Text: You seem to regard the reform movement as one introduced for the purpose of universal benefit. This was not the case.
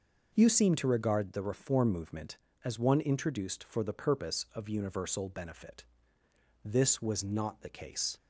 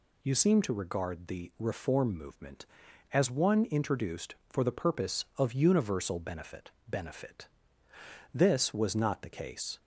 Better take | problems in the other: first | says "benefit" twice; at 6.8 s

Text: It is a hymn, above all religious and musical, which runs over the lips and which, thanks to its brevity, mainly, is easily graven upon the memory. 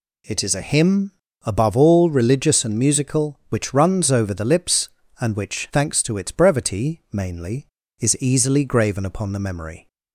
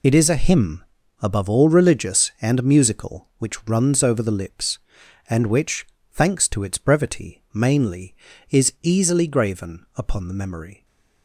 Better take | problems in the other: first | loses the start of "It"; at 0.0 s; 45 ms

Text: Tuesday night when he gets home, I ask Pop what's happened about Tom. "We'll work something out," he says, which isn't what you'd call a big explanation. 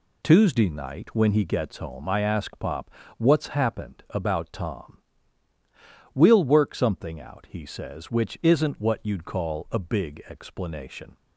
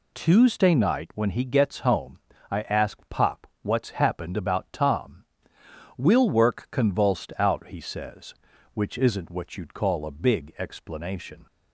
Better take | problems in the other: first | pauses between "Pop" and "what's"; slight; at 3.4 s; 0.16 s long; slight in the first // says "convulsed" for "something"; at 6.6 s

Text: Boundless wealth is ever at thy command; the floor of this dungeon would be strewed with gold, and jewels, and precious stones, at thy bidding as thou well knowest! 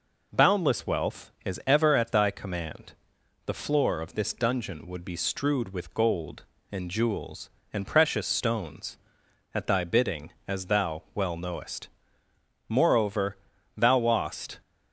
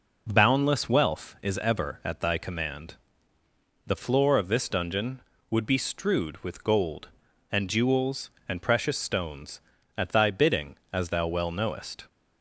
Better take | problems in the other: second | goes on to say "Moreover thou wast"; strong; from 12.6 s on; 1.9 s long

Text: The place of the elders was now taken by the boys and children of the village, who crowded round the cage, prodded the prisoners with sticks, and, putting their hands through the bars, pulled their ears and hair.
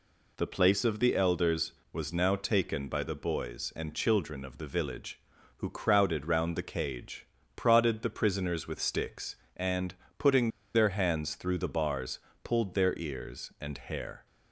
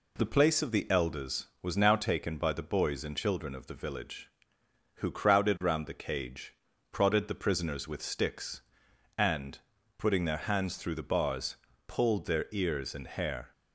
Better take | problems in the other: second | pauses between "putting" and "their"; slight; at 10.4 s; 0.25 s long

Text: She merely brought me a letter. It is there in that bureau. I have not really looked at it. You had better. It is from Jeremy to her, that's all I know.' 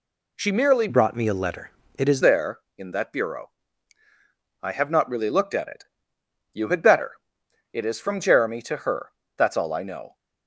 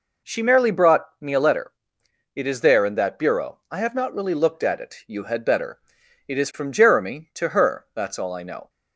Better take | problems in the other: second | changes voice from "brought" to "is"; from 0.8 to 2.2 s; 1.4 s long

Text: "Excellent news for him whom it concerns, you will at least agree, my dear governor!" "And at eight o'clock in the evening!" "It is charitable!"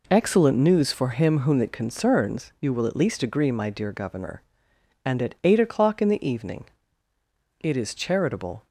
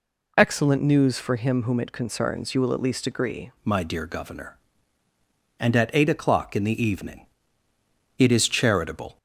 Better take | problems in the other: first | changes voice at "my"; from 3.6 s on; 5.5 s long

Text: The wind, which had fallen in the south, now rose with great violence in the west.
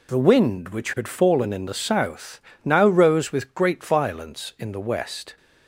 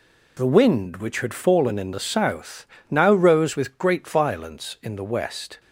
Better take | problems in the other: neither | none

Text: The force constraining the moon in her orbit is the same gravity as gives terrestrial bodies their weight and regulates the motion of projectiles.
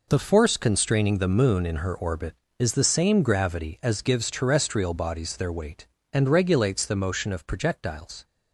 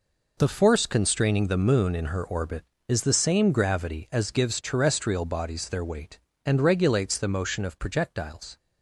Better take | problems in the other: neither | none

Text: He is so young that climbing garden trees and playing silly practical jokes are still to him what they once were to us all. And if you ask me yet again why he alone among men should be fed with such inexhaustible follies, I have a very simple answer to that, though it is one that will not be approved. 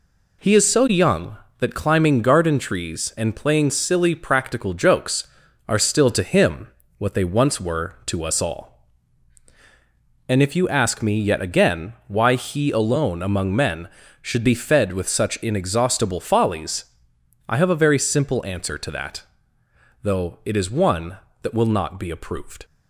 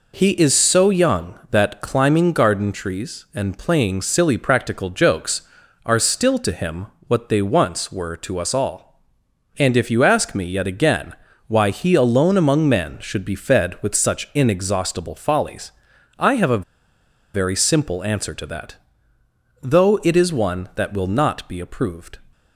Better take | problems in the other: first | pauses between "him" and "what"; slight; at 6.8 s; 0.22 s long; slight in the first // pauses between "again" and "why"; slight; at 11.1 s; 0.34 s long // pauses between "a" and "very"; noticeable; at 16.6 s; 0.73 s long

